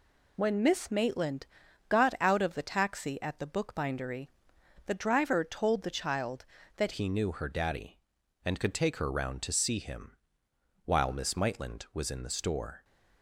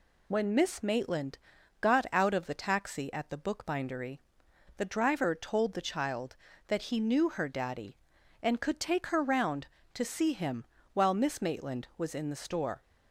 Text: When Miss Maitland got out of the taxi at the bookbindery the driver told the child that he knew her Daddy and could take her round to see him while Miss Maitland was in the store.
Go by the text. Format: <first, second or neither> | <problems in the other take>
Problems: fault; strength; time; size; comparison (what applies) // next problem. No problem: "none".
second | pauses between "Maitland" and "got"; at 1.4 s; 0.42 s long; also in the second // pauses between "bookbindery" and "the"; noticeable; at 4.2 s; 0.60 s long; noticeable in the second // changes voice at "he"; from 6.9 s on; 5.9 s long // pauses between "him" and "while"; noticeable; at 10.1 s; 0.70 s long; slight in the second